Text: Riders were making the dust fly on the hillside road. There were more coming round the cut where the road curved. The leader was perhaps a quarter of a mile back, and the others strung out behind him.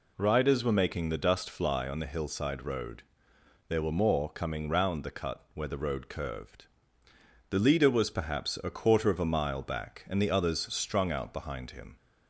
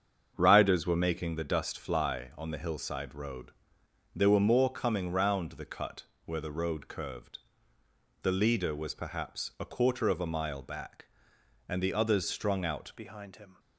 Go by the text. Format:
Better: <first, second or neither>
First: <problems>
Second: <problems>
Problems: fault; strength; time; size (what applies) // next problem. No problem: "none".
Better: first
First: none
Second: starts louder than the rest; strong; until 1.3 s; 7 dB // pauses between "cut" and "where"; slight; at 6.0 s; 0.22 s long // changes voice at "behind"; from 12.9 s on; 0.6 s long